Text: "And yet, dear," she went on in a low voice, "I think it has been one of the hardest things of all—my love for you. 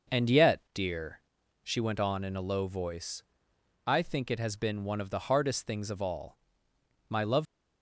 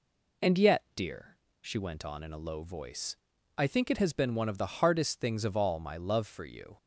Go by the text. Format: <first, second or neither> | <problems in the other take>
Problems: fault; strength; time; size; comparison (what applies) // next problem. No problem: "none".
second | stops before "for you"; at 7.4 s